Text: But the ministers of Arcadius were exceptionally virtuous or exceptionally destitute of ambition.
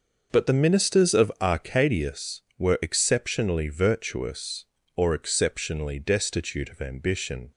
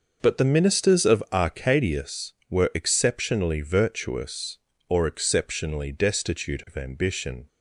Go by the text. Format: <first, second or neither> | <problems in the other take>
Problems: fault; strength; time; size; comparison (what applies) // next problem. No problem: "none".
neither | starts louder than the rest; noticeable; the same in both